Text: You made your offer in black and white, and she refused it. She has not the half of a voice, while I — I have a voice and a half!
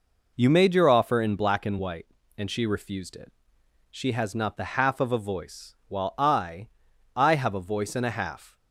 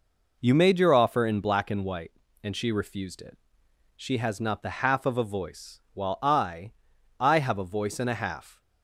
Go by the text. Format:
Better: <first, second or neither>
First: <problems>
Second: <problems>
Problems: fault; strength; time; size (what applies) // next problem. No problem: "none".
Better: neither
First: none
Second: none